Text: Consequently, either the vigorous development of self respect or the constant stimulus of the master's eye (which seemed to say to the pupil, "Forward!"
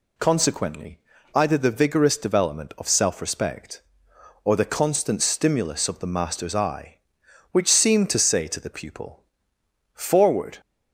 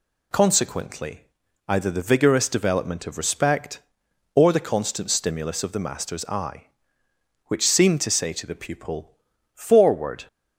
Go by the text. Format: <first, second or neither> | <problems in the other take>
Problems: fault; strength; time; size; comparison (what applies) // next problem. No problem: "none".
first | skips "self"; at 3.1 s